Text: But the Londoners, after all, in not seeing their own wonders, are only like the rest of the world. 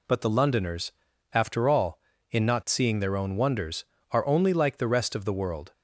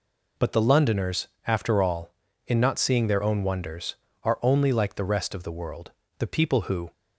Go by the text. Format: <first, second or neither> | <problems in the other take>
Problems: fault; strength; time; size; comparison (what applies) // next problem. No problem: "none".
first | goes on to say "The people who"; noticeable; from 6.1 s on; 0.74 s long